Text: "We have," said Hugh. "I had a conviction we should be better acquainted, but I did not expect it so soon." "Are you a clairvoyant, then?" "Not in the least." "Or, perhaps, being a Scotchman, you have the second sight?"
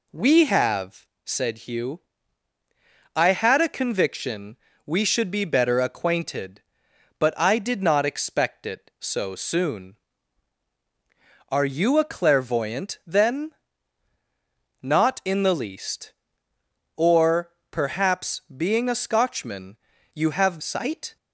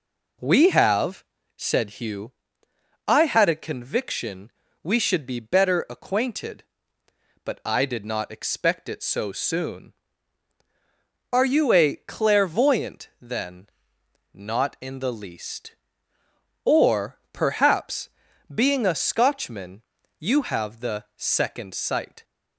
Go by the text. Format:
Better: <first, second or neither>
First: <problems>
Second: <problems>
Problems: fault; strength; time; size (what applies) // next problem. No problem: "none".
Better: second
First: pauses between "conviction" and "we"; slight; at 4.5 s; 0.30 s long // skips "the second"; at 20.6 s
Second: pauses between "conviction" and "we"; slight; at 4.5 s; 0.32 s long